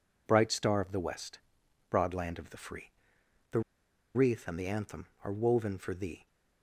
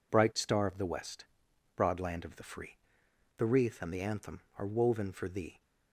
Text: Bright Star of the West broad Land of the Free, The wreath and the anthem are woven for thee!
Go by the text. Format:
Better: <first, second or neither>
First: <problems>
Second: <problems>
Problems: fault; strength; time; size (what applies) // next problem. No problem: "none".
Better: second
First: pauses between "West" and "broad"; noticeable; at 1.3 s; 0.50 s long // pauses between "The" and "wreath"; noticeable; at 3.5 s; 0.54 s long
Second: pauses between "West" and "broad"; noticeable; at 1.2 s; 0.50 s long